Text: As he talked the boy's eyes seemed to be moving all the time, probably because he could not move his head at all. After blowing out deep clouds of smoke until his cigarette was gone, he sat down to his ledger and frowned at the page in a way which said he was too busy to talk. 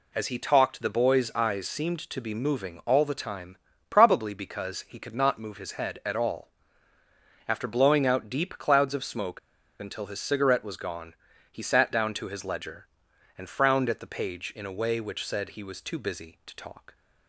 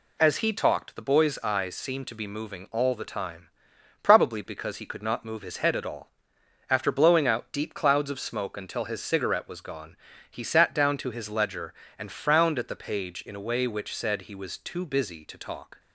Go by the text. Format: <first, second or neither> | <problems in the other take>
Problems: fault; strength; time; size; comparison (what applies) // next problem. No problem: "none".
second | pauses between "smoke" and "until"; at 9.3 s; 0.41 s long